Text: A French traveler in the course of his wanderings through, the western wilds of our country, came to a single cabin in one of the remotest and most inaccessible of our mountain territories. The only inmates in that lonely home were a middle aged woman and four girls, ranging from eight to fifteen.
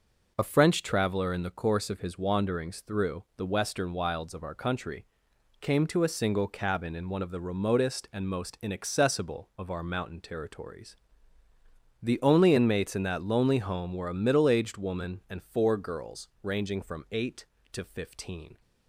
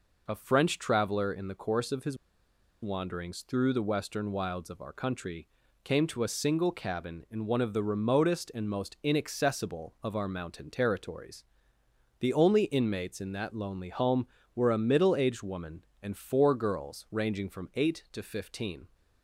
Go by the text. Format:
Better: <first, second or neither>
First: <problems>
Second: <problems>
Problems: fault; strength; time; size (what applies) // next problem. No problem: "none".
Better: first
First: none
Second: pauses between "his" and "wanderings"; noticeable; at 2.1 s; 0.66 s long